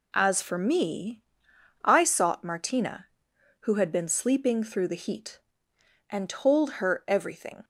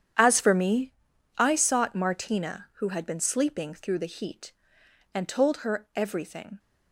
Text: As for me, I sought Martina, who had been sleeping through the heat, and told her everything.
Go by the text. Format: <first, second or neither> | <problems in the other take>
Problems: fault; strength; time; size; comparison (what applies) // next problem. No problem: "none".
first | gets quieter; strong; throughout; 14 dB